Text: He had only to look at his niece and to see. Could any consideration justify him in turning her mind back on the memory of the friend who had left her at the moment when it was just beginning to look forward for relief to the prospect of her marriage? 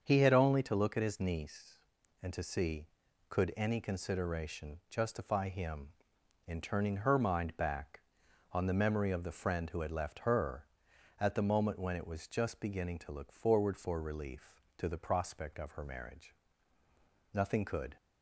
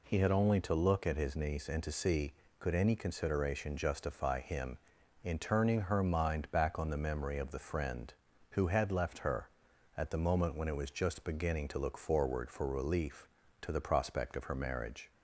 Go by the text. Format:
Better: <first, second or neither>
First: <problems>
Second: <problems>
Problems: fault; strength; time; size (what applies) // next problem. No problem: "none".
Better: second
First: starts louder than the rest; until 1.0 s; 7 dB // goes on to say "Nothing could"; noticeable; from 17.3 s on; 0.62 s long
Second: none